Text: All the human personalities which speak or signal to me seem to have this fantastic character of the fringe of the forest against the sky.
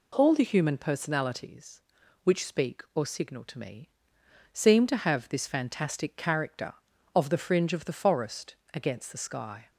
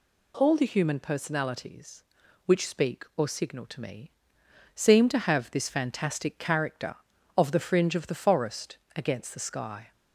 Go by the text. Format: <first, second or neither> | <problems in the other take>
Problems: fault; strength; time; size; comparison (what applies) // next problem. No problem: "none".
second | starts louder than the rest; slight; until 1.5 s; 2.5 dB // pauses between "me" and "seem"; noticeable; at 3.8 s; 0.62 s long; noticeable in the second // pauses between "forest" and "against"; slight; at 8.5 s; 0.22 s long; slight in the second